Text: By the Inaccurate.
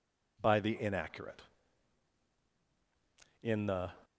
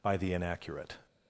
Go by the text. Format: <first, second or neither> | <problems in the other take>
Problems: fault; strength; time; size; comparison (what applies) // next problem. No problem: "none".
second | goes on to say "In the"; from 3.4 s on; 0.50 s long